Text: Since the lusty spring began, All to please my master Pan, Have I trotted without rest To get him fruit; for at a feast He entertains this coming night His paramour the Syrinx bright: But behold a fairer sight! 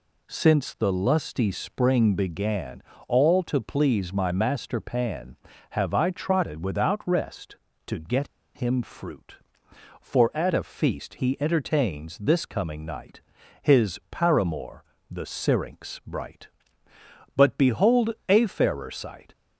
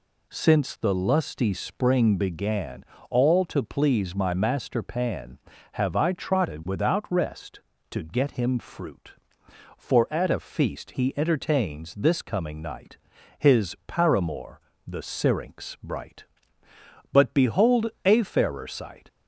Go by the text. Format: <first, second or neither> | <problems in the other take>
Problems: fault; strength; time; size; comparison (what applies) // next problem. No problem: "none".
second | pauses between "get" and "him"; slight; at 8.2 s; 0.27 s long // pauses between "night" and "His"; at 13.2 s; 0.42 s long; also in the second // pauses between "paramour" and "the"; slight; at 14.8 s; 0.26 s long; slight in the second // pauses between "behold" and "a"; slight; at 18.1 s; 0.16 s long; slight in the second